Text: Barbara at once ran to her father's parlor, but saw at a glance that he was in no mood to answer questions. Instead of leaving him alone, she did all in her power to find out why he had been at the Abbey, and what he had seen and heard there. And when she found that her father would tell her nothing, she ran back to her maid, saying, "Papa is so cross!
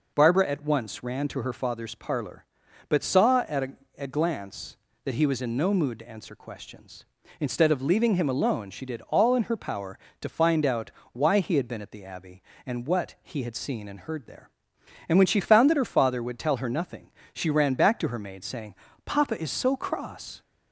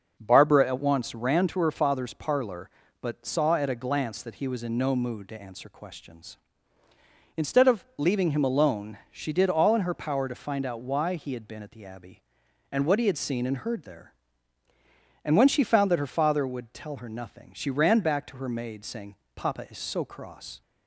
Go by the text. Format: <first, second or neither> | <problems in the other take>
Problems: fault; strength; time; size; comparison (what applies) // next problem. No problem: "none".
second | says "a" twice; at 3.9 s // pauses between "out" and "why"; slight; at 10.8 s; 0.22 s long